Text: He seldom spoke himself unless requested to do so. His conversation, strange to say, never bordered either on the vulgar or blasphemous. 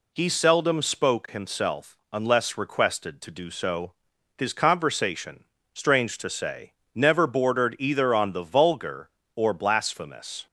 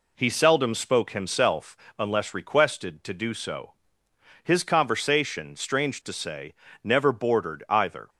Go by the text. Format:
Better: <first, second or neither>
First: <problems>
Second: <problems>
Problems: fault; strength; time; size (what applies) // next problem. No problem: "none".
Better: first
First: pauses between "himself" and "unless"; slight; at 1.9 s; 0.16 s long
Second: pauses between "himself" and "unless"; slight; at 1.7 s; 0.22 s long // stops before "on the vulgar or blasphemous"; at 8.0 s